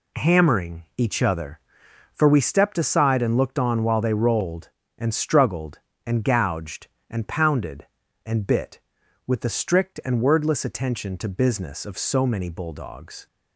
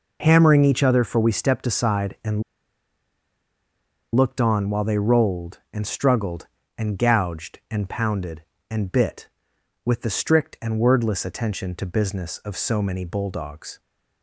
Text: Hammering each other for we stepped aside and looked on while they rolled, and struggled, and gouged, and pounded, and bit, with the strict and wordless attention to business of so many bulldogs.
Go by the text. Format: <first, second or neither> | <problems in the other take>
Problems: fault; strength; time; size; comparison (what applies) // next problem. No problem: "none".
first | pauses between "and" and "looked"; strong; at 2.4 s; 1.7 s long